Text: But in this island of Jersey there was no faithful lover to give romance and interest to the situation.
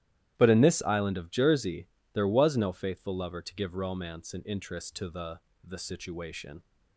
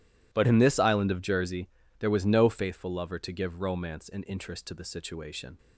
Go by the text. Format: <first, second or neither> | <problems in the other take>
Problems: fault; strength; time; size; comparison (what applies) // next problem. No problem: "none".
second | starts louder than the rest; strong; until 1.3 s; 13 dB // pauses between "Jersey" and "there"; slight; at 1.8 s; 0.26 s long; slight in the second // says "the" twice; at 5.6 s